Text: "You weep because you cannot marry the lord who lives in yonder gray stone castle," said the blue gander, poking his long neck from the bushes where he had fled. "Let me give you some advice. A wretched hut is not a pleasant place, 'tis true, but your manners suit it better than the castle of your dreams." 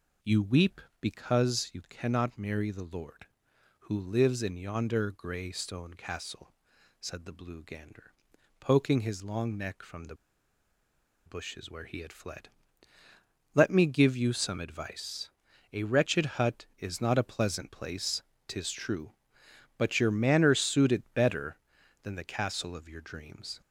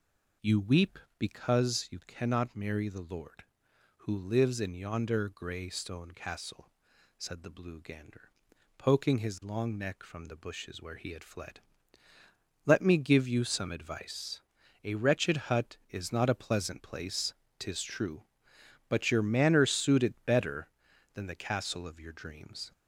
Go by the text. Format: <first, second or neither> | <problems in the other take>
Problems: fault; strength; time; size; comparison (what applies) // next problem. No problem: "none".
second | pauses between "the" and "bushes"; at 10.1 s; 1.1 s long